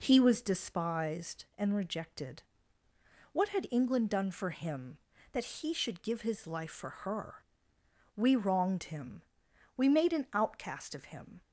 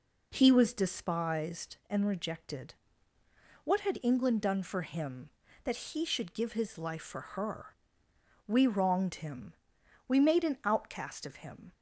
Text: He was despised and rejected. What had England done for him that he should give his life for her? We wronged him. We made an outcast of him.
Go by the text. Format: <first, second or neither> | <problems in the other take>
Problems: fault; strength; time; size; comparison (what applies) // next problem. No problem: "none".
neither | none